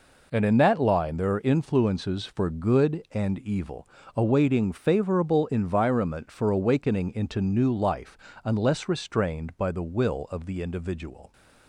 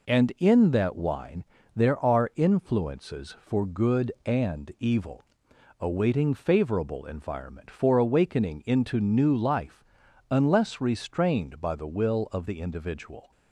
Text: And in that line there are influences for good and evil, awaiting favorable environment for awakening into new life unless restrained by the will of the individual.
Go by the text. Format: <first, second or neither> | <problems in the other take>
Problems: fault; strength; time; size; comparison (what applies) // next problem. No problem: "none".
first | says "wine" for "line"; at 0.9 s // pauses between "life" and "unless"; noticeable; at 9.8 s; 0.48 s long; slight in the first